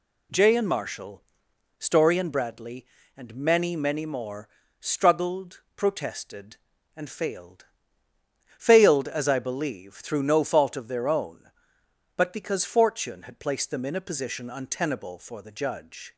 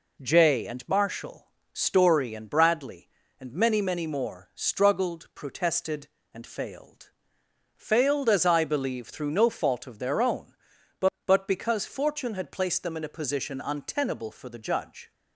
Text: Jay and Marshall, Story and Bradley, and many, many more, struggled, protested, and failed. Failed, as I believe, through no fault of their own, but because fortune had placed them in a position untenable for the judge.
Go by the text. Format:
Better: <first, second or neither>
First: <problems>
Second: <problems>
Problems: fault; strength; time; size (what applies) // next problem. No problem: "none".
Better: first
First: none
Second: says "but" twice; at 11.2 s